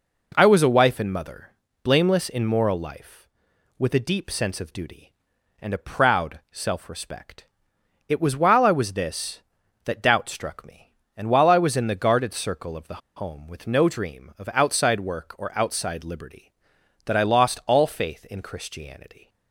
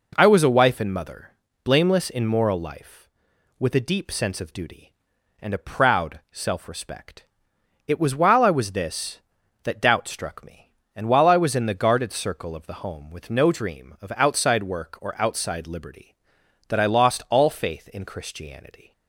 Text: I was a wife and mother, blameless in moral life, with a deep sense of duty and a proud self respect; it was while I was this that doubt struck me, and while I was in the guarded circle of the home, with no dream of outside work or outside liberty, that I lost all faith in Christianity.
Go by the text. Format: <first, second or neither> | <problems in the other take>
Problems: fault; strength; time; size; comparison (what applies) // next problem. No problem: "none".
second | pauses between "the" and "home"; slight; at 13.0 s; 0.16 s long